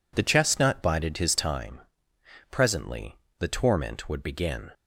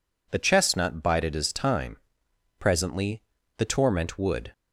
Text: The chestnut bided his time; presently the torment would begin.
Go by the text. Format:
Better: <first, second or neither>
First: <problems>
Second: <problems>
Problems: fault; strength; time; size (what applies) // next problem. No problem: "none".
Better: first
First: pauses between "presently" and "the"; slight; at 3.1 s; 0.24 s long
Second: pauses between "presently" and "the"; slight; at 3.2 s; 0.34 s long // stops before "begin"; at 4.5 s